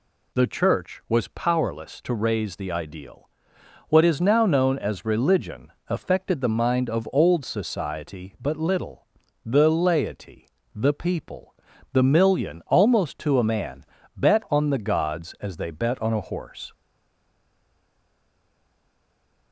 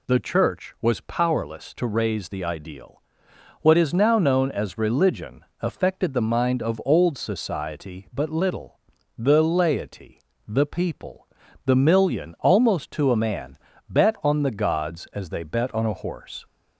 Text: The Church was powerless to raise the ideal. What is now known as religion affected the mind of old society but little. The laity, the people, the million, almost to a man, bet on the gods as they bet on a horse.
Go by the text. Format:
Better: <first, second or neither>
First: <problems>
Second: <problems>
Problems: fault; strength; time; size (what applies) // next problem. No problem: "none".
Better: second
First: pauses between "religion" and "affected"; slight; at 5.7 s; 0.16 s long // stays silent after the last word; strong; from 16.7 s on; 2.8 s long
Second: pauses between "religion" and "affected"; slight; at 5.4 s; 0.16 s long